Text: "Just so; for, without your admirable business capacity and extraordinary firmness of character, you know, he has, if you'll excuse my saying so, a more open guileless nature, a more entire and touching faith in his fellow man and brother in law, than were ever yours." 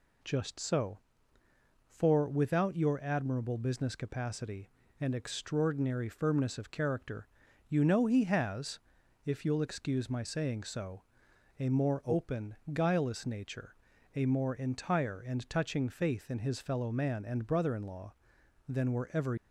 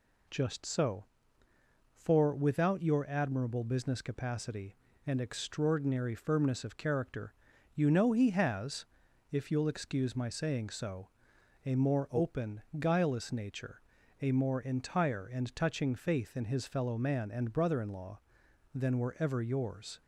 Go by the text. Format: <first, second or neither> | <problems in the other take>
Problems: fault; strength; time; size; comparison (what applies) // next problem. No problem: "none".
second | pauses between "open" and "guileless"; slight; at 12.5 s; 0.16 s long; slight in the second // stops before "yours"; at 19.3 s